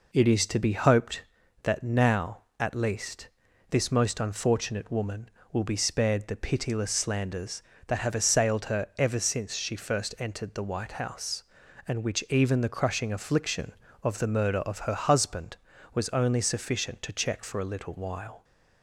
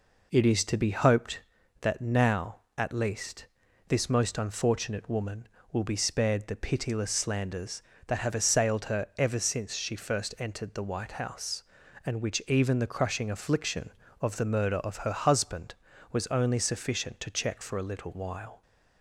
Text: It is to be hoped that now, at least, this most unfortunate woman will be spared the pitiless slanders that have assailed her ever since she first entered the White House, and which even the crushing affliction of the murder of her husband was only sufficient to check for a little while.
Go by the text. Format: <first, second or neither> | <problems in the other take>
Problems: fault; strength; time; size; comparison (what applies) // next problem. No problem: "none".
neither | none